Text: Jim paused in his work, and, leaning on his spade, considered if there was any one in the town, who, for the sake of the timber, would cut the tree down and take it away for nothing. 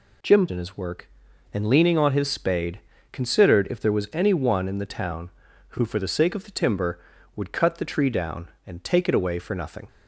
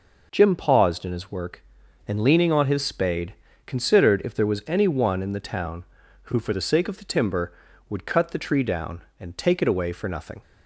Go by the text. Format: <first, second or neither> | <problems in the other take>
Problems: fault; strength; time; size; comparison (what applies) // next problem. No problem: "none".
second | skips "paused"; at 0.4 s